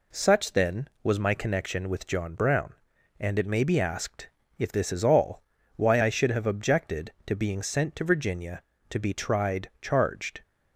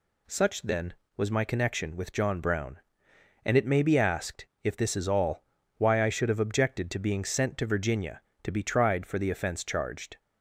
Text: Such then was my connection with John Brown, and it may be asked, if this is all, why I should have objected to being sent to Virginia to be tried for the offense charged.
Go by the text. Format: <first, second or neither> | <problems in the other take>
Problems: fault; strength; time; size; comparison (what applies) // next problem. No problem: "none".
second | skips "for the offense"; at 9.7 s